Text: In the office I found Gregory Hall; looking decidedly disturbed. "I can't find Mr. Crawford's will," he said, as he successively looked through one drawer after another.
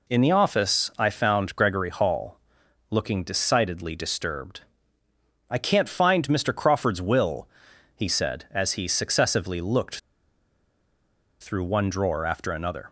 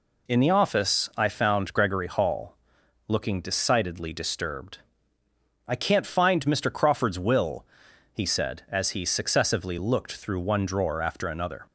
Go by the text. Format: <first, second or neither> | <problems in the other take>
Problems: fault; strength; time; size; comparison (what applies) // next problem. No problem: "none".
second | pauses between "looked" and "through"; strong; at 9.9 s; 1.4 s long